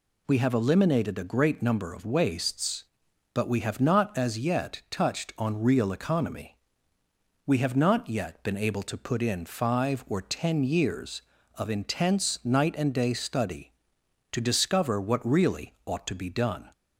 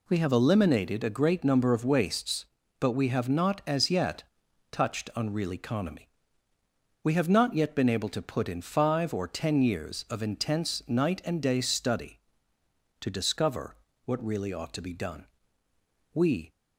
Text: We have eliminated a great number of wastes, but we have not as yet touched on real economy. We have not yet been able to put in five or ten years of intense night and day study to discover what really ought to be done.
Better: first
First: none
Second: pauses between "yet" and "touched"; noticeable; at 4.2 s; 0.48 s long // pauses between "discover" and "what"; slight; at 13.7 s; 0.30 s long // goes on to say "We"; slight; from 16.1 s on; 0.38 s long

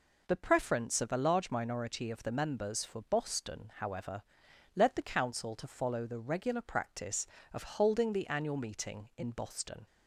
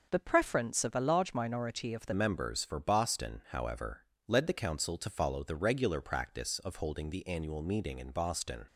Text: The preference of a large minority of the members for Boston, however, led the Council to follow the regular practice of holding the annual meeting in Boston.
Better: first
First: none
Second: changes voice at "members"; from 2.1 s on; 6.5 s long

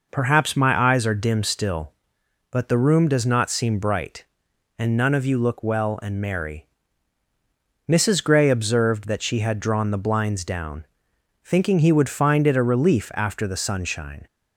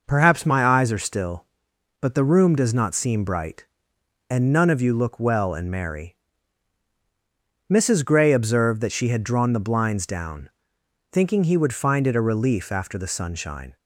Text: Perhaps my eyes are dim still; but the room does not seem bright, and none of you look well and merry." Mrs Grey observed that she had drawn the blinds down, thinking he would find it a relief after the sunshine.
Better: first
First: none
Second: skips "dim"; at 0.9 s

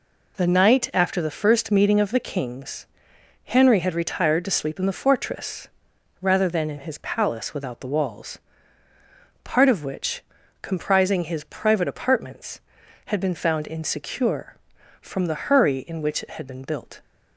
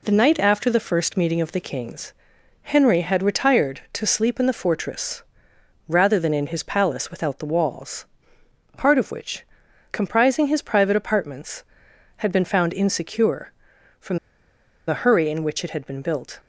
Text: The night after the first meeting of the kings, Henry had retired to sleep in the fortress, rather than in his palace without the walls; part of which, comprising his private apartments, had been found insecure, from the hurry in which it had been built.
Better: first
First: none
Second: pauses between "from" and "the"; noticeable; at 14.1 s; 0.69 s long

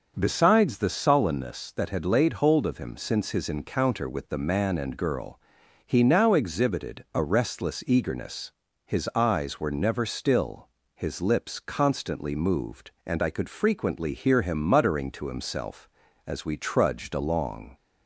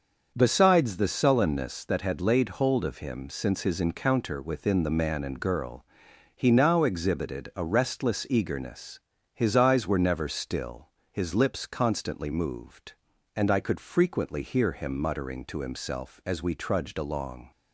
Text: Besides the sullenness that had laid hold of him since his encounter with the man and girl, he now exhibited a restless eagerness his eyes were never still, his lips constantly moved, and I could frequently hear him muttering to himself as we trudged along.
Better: first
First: starts louder than the rest; until 1.1 s; 6.5 dB // pauses between "eagerness" and "his"; slight; at 8.5 s; 0.32 s long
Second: starts louder than the rest; until 1.3 s; 6.5 dB // says "within" for "with"; at 4.4 s // pauses between "eagerness" and "his"; slight; at 8.9 s; 0.36 s long

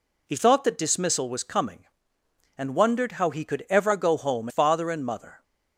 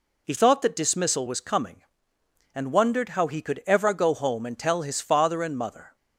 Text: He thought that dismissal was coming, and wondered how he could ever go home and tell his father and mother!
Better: second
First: skips "and tell his"; at 4.4 s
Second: none

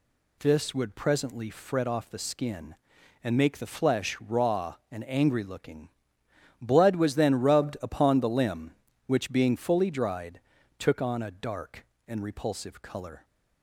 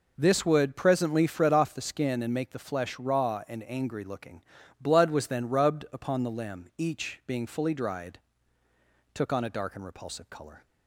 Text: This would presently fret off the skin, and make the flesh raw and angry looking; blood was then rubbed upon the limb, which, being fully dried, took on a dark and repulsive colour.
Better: first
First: none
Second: says "each" for "which"; at 6.7 s

